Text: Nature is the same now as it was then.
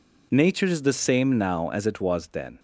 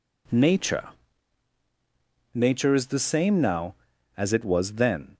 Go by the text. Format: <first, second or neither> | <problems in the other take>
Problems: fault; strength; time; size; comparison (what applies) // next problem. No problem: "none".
first | says "Nature" twice; at 2.3 s